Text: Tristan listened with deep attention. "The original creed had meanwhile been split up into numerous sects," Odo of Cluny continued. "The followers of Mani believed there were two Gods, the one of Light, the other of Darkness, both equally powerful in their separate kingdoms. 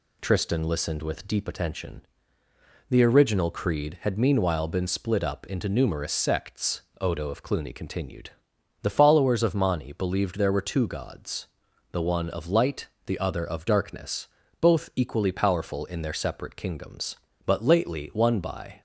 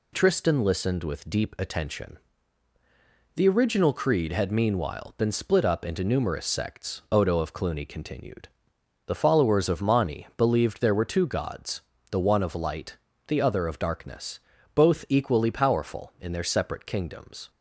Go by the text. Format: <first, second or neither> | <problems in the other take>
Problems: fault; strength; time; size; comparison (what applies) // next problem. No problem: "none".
second | goes on to say "But lately one by"; from 17.4 s on; 1.3 s long